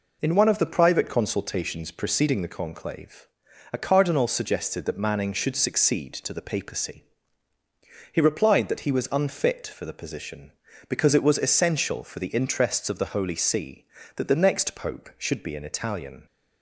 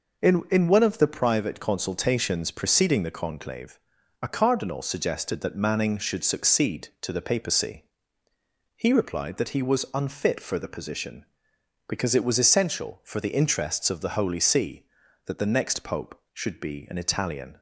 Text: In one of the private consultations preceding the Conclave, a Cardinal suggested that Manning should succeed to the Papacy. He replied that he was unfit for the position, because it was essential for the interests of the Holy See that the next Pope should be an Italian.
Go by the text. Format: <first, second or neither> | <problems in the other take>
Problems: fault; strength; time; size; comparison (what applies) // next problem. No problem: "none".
first | says "In" twice; at 0.4 s